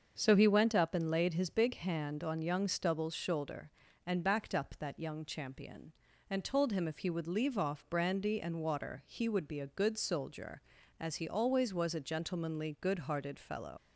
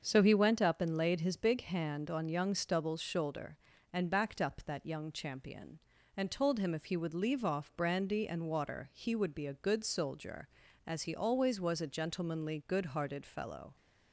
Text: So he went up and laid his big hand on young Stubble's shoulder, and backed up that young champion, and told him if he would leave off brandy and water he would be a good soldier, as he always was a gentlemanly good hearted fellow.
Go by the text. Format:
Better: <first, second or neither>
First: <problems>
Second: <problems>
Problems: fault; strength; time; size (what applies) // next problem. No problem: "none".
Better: second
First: starts louder than the rest; until 1.1 s; 6.5 dB // leaves "fellow" unfinished; at 13.7 s; 110 ms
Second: starts louder than the rest; until 1.0 s; 6.5 dB